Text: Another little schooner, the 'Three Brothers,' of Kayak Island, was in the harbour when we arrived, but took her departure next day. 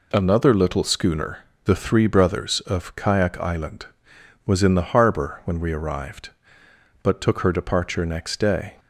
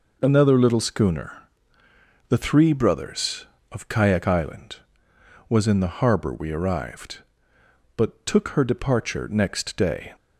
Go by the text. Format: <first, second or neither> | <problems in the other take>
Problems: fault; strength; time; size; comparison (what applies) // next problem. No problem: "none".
first | skips "when"; at 6.3 s